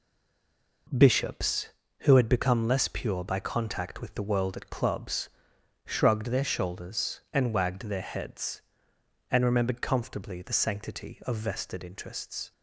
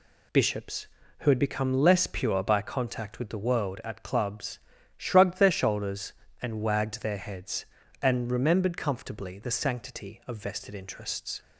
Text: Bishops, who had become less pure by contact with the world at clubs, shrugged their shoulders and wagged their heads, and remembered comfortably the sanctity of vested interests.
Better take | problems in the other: second | stays silent before the first word; slight; until 0.8 s; 0.8 s long

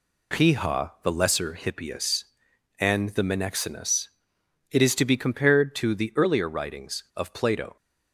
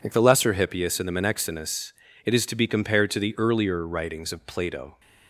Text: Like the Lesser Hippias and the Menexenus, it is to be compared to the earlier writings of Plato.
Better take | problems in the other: second | says "Piha" for "Like"; at 0.3 s

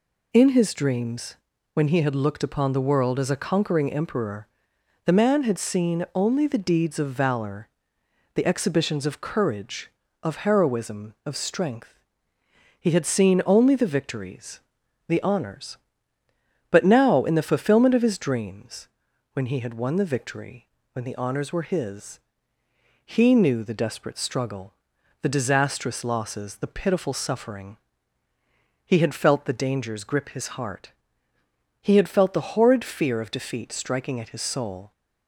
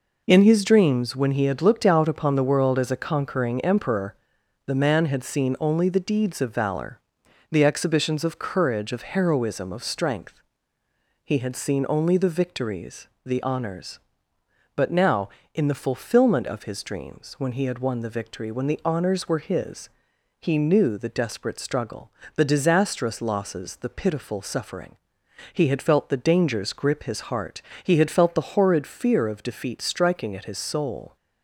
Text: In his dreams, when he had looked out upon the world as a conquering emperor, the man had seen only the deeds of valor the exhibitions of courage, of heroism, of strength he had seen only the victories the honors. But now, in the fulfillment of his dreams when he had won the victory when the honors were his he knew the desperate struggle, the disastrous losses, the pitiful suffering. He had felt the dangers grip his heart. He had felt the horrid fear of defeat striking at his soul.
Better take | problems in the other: second | skips "out"; at 2.4 s // pauses between "valor" and "the"; noticeable; at 7.6 s; 0.66 s long; noticeable in the second // pauses between "strength" and "he"; noticeable; at 11.9 s; 0.80 s long; noticeable in the second // pauses between "victories" and "the"; noticeable; at 14.5 s; 0.48 s long; slight in the second // pauses between "dreams" and "when"; noticeable; at 18.8 s; 0.46 s long // pauses between "victory" and "when"; slight; at 20.6 s; 0.28 s long // pauses between "his" and "he"; noticeable; at 22.1 s; 0.84 s long; noticeable in the second

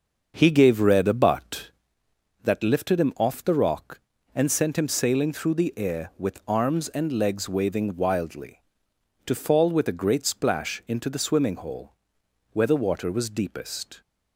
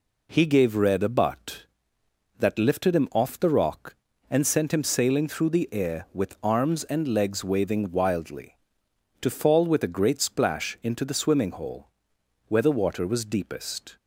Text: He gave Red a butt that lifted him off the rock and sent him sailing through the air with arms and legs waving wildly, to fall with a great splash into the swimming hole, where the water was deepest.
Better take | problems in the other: second | starts louder than the rest; until 2.0 s; 6.5 dB

